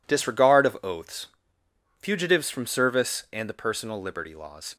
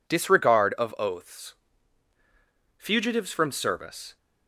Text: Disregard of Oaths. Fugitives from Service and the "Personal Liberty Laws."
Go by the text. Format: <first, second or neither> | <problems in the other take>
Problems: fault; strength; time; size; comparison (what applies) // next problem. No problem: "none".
first | stops before "and the Personal Liberty Laws"; at 4.1 s